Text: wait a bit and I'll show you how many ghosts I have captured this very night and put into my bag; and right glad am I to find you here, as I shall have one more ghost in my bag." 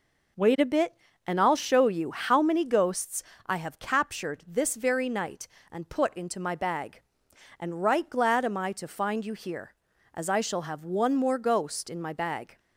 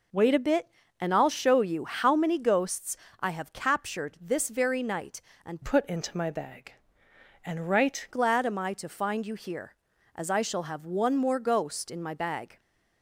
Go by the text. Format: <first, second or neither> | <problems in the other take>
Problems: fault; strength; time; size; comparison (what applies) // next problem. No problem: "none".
first | pauses between "ghosts" and "I"; slight; at 2.9 s; 0.24 s long; slight in the first // changes voice from "put" to "right"; from 5.6 to 8.0 s; 2.4 s long